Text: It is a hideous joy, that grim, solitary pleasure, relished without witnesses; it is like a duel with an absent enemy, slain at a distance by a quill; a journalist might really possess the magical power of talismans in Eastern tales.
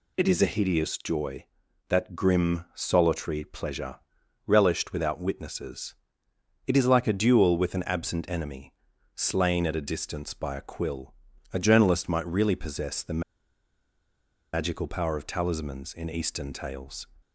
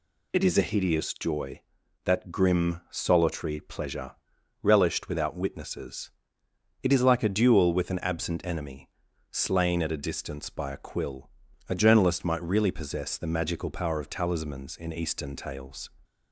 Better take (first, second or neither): second